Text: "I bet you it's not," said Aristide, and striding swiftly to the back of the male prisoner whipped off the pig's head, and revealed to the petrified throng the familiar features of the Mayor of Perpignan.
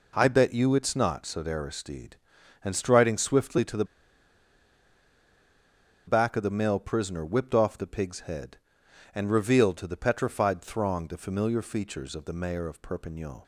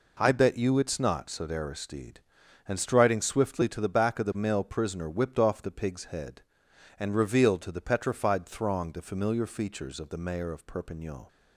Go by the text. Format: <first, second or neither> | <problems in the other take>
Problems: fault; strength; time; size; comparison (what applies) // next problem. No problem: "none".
second | pauses between "the" and "back"; strong; at 3.8 s; 2.2 s long